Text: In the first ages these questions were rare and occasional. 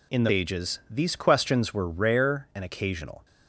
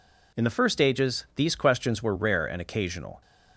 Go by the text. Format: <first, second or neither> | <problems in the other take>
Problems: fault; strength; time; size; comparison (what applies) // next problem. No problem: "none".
second | skips "first"; at 0.3 s